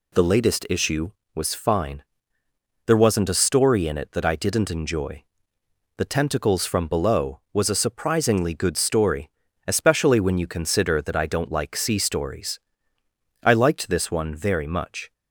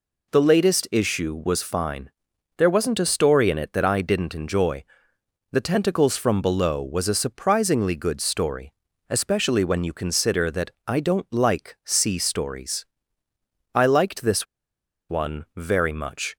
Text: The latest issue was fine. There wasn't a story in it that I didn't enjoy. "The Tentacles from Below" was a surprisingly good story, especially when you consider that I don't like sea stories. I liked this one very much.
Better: first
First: none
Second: pauses between "that" and "I"; slight; at 10.7 s; 0.16 s long // pauses between "this" and "one"; noticeable; at 14.4 s; 0.65 s long

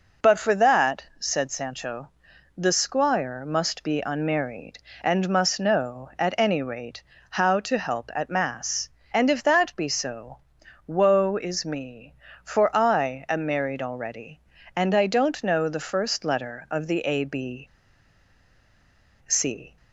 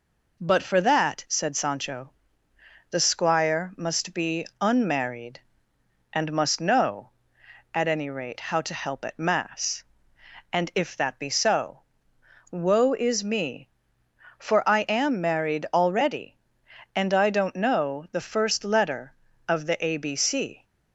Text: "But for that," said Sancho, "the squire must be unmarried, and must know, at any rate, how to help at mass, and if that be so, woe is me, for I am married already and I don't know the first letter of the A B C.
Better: second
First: pauses between "B" and "C"; strong; at 17.6 s; 1.6 s long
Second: none

